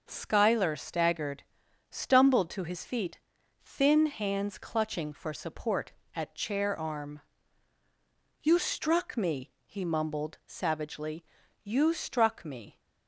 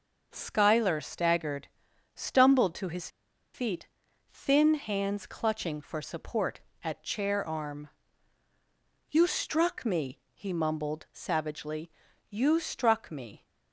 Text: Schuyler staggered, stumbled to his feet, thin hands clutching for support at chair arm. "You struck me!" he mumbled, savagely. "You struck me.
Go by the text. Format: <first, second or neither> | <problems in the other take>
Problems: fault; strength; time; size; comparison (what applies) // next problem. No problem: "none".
first | pauses between "his" and "feet"; at 3.0 s; 0.44 s long